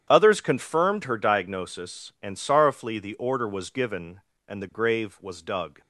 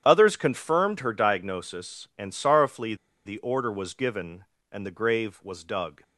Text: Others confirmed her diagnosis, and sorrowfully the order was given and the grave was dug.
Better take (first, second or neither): first